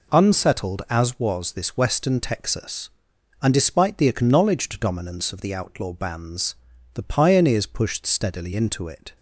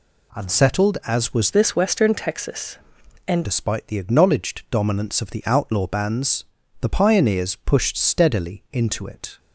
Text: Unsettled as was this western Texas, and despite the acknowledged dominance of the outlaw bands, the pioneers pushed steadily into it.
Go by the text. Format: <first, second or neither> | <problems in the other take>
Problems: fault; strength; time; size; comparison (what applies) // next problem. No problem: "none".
first | changes voice from "this" to "and"; from 1.5 to 3.4 s; 1.9 s long